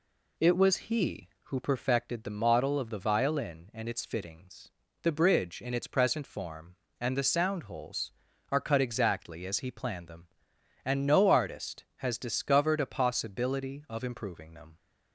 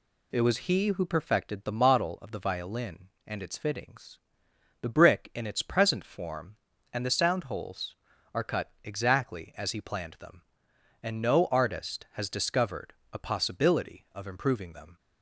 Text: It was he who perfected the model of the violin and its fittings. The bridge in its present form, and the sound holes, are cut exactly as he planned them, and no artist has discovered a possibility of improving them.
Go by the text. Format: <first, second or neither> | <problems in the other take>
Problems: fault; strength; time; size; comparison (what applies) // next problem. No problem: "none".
first | says "brick" for "bridge"; at 4.8 s // pauses between "discovered" and "a"; slight; at 12.9 s; 0.18 s long